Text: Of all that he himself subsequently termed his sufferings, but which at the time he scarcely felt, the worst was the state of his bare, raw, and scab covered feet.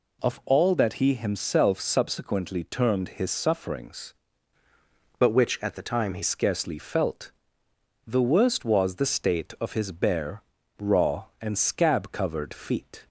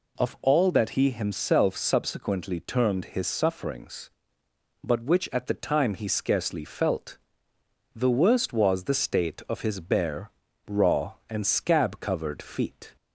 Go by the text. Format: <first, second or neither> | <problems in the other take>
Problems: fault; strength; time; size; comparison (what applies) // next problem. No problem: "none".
second | changes voice from "but" to "he"; from 5.2 to 6.2 s; 1.0 s long